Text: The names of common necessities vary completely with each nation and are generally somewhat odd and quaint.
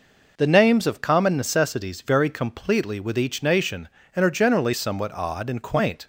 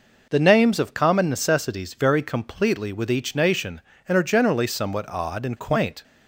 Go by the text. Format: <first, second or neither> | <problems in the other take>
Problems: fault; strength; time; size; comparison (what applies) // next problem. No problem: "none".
neither | none